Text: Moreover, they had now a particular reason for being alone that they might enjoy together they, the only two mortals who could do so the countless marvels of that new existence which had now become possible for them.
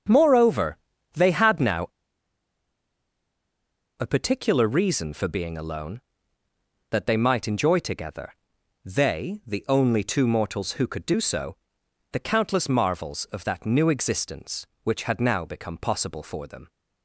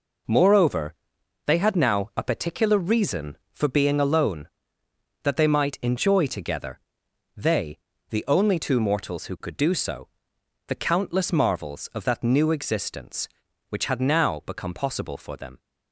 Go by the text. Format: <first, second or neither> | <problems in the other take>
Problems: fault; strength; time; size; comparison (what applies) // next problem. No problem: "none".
second | starts louder than the rest; until 1.4 s; 7 dB // pauses between "now" and "a"; strong; at 1.8 s; 2.0 s long // pauses between "together" and "they"; noticeable; at 8.3 s; 0.54 s long; noticeable in the second // pauses between "so" and "the"; noticeable; at 11.5 s; 0.56 s long; noticeable in the second